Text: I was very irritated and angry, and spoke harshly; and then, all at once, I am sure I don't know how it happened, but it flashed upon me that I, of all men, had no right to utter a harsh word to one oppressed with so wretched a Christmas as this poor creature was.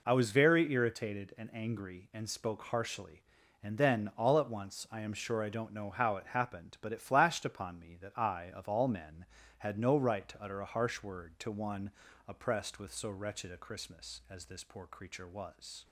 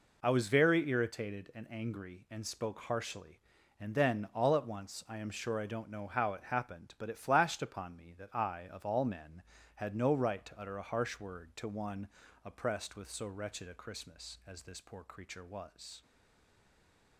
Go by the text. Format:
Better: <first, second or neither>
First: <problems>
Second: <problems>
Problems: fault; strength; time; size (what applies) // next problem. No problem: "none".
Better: first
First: pauses between "one" and "oppressed"; slight; at 11.9 s; 0.36 s long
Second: pauses between "one" and "oppressed"; slight; at 12.0 s; 0.36 s long // stays silent after the last word; noticeable; from 16.0 s on; 1.1 s long